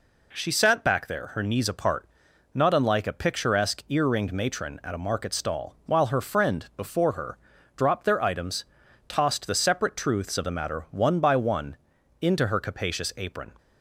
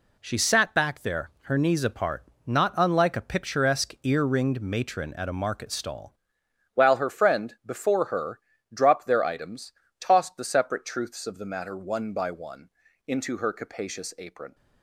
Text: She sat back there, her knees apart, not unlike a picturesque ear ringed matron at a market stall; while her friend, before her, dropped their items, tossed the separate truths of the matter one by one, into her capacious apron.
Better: first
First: none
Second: changes voice at "while"; from 6.7 s on; 7.8 s long

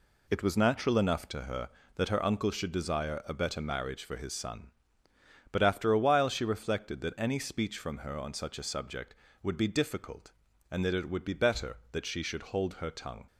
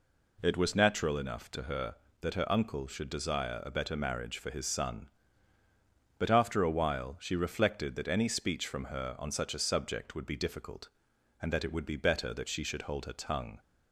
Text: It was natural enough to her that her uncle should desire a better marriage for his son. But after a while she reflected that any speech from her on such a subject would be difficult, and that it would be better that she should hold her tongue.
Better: neither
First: none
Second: none

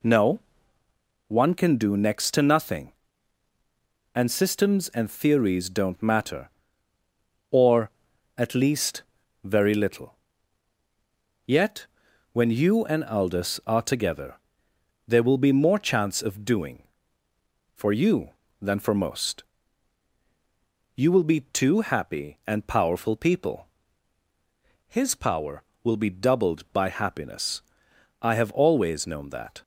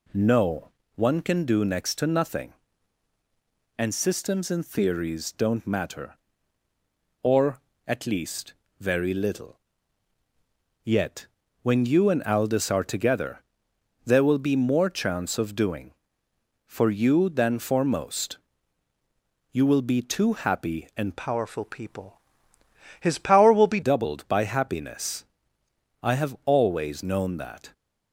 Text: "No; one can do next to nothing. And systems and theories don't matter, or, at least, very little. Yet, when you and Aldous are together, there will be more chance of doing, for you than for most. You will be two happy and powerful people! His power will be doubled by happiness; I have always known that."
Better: first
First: none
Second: changes voice from "powerful" to "be"; from 21.1 to 23.8 s; 2.7 s long

